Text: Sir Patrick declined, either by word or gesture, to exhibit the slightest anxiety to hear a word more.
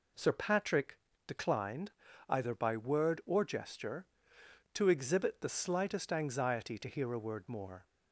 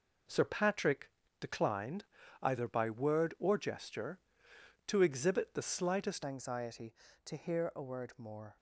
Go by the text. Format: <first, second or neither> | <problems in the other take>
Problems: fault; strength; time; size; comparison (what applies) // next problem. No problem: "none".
first | pauses between "Patrick" and "declined"; slight; at 1.0 s; 0.30 s long; slight in the first // changes voice at "anxiety"; from 6.2 s on; 2.3 s long